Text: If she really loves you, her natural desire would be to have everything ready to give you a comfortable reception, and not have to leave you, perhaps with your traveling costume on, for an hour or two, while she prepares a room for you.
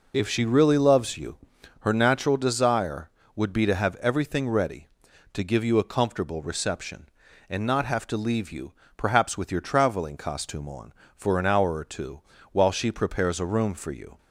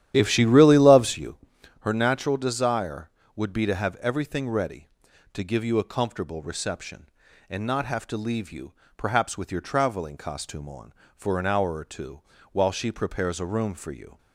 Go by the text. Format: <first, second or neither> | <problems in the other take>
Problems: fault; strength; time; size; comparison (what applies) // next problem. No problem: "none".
first | starts louder than the rest; strong; until 1.3 s; 11.5 dB